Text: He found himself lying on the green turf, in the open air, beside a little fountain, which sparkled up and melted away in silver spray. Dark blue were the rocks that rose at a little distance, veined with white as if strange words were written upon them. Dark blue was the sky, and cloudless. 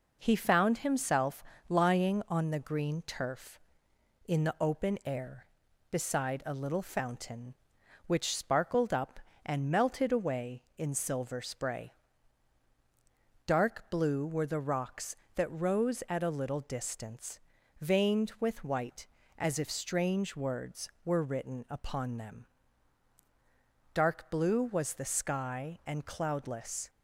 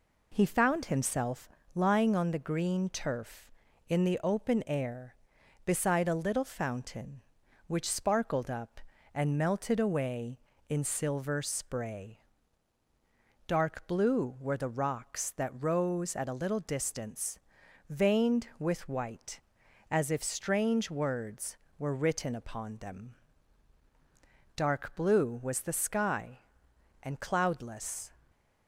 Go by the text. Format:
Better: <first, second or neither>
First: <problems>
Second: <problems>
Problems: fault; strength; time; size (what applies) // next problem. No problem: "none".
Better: neither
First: pauses between "himself" and "lying"; slight; at 1.4 s; 0.28 s long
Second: pauses between "himself" and "lying"; slight; at 1.4 s; 0.28 s long